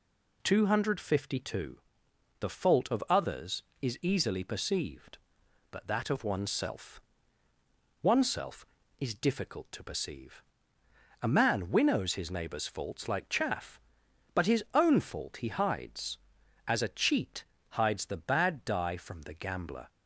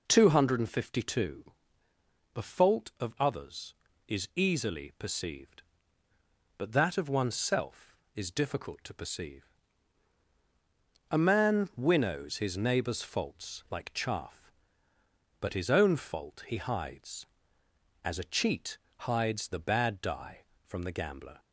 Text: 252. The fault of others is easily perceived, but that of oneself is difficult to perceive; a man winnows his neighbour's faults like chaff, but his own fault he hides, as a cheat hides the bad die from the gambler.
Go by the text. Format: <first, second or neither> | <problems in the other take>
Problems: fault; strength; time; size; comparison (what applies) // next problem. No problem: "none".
second | says "oneself" twice; at 8.0 s // pauses between "cheat" and "hides"; slight; at 17.4 s; 0.28 s long; slight in the second